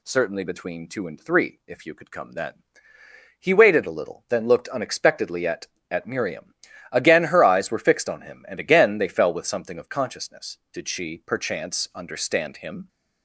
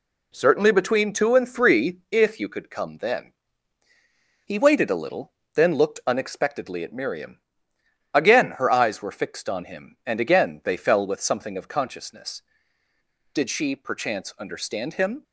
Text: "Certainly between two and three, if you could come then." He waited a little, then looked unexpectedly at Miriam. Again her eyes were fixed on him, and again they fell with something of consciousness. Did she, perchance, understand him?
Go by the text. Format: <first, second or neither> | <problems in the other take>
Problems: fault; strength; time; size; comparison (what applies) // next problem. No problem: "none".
second | says "at" twice; at 5.9 s